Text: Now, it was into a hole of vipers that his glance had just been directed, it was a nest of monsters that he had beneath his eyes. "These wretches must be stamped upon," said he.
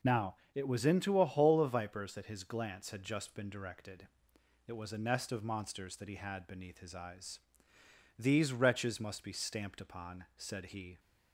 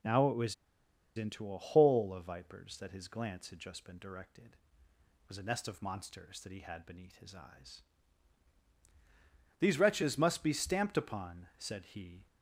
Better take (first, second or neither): first